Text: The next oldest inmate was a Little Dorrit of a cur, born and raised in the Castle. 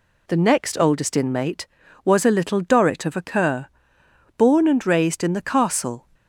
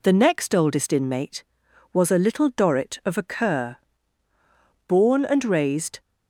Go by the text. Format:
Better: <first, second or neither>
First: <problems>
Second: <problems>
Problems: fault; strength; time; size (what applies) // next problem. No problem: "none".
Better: first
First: none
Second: stops before "in the Castle"; at 6.0 s